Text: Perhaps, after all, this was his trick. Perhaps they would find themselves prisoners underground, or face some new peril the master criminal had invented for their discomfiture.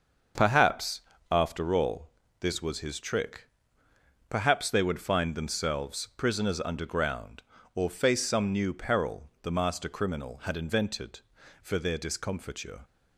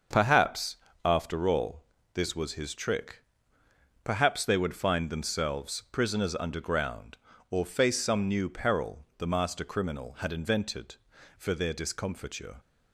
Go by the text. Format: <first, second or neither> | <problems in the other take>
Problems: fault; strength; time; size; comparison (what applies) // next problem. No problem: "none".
neither | starts louder than the rest; the same in both